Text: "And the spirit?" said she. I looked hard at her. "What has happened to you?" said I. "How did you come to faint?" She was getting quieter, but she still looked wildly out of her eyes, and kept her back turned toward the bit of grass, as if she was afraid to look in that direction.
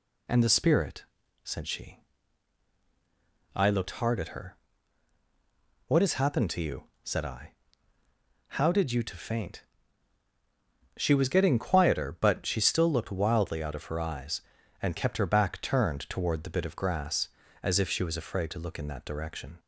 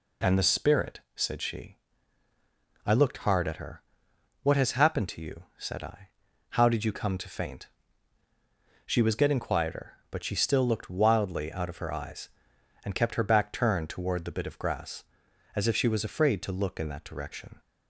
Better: second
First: skips "come"; at 9.0 s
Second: none

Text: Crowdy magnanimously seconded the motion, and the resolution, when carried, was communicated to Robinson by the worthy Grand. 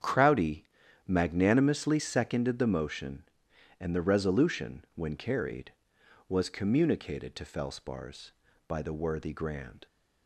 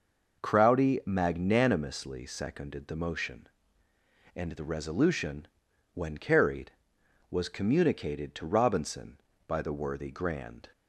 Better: second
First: starts louder than the rest; strong; until 1.4 s; 8 dB // pauses between "Crowdy" and "magnanimously"; at 0.6 s; 0.40 s long // says "Felspars" for "Robinson"; at 7.4 s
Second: none

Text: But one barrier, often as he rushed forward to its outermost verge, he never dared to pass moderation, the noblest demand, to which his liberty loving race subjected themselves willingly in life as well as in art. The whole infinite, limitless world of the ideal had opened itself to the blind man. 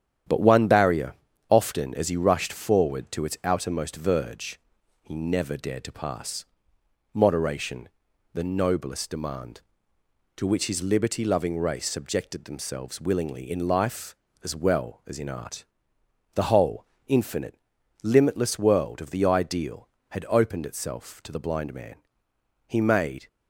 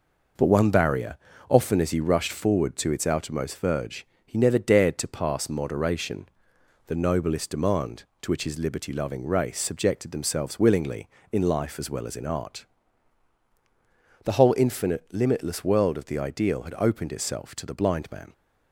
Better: second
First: starts louder than the rest; strong; until 1.6 s; 9.5 dB // pauses between "pass" and "moderation"; noticeable; at 6.4 s; 0.68 s long // pauses between "whole" and "infinite"; slight; at 16.8 s; 0.22 s long // goes on to say "He made"; from 22.6 s on; 0.60 s long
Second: none

